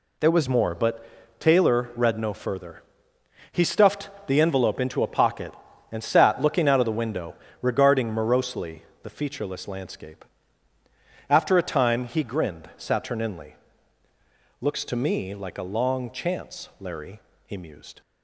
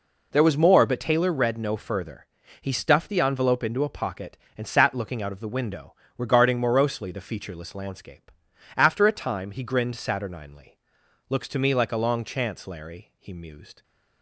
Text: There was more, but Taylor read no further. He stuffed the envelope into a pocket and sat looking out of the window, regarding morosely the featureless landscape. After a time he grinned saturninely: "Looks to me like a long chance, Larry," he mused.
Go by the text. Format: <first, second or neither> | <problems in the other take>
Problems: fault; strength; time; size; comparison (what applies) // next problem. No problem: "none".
second | changes voice at "more"; from 0.4 s on; 17.6 s long // pauses between "stuffed" and "the"; slight; at 4.0 s; 0.18 s long // pauses between "morosely" and "the"; slight; at 8.8 s; 0.20 s long